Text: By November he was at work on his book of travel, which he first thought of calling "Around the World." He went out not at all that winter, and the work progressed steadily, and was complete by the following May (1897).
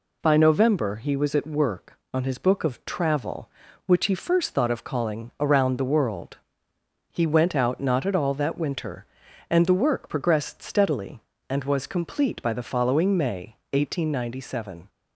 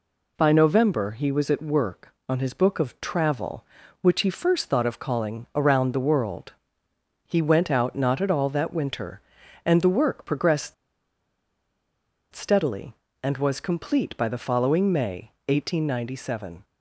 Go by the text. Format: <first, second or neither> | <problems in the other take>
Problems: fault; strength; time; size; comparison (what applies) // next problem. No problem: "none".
first | pauses between "progressed" and "steadily"; strong; at 10.7 s; 1.5 s long